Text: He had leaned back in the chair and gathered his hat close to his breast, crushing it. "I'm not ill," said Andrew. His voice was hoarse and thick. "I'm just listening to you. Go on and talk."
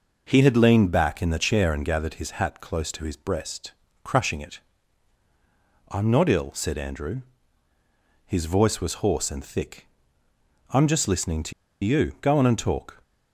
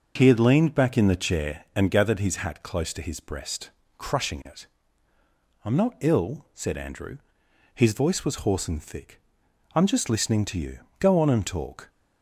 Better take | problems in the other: second | pauses between "to" and "you"; slight; at 11.5 s; 0.31 s long

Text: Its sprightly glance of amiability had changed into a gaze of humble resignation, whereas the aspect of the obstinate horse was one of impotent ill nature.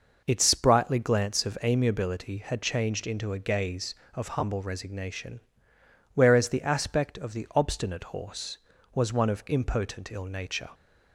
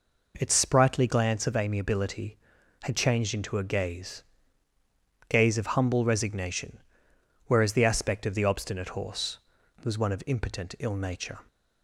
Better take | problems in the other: first | says "gaze" twice; at 5.2 s

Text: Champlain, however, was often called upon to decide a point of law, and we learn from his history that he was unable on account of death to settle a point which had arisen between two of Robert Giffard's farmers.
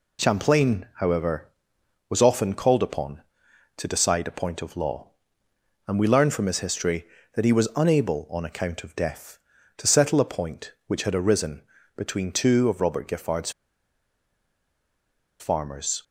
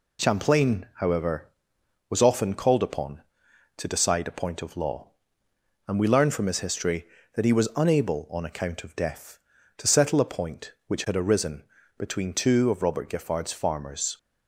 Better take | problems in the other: second | pauses between "arisen" and "between"; slight; at 11.6 s; 0.34 s long; slight in the second // pauses between "Giffard's" and "farmers"; strong; at 13.4 s; 1.8 s long

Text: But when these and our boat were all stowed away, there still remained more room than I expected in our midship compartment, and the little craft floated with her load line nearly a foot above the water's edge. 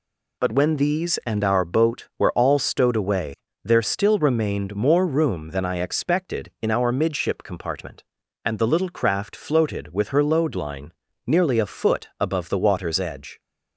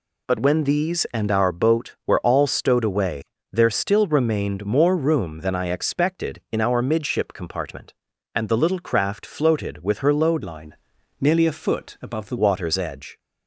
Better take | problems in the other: first | changes voice from "line" to "the"; from 10.4 to 12.3 s; 1.9 s long // pauses between "line" and "nearly"; at 10.7 s; 0.44 s long; slight in the first

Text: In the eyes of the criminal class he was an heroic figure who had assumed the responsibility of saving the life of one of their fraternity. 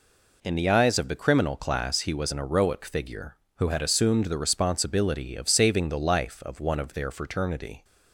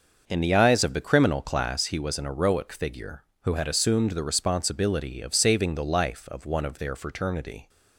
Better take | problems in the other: first | starts louder than the rest; until 1.8 s; 6 dB

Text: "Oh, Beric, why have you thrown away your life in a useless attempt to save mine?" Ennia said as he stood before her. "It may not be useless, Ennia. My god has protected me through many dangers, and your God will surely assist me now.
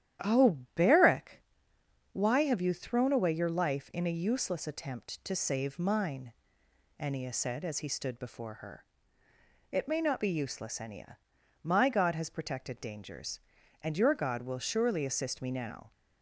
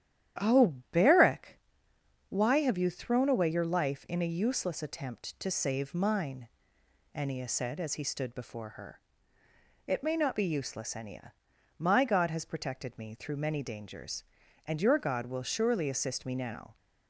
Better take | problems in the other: second | starts louder than the rest; strong; until 1.3 s; 11 dB; strong in the second // skips "me through many"; at 12.8 s

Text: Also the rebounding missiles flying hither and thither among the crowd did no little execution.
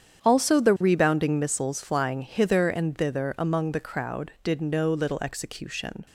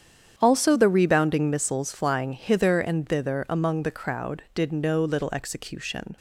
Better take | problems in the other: neither | starts louder than the rest; strong; the same in both

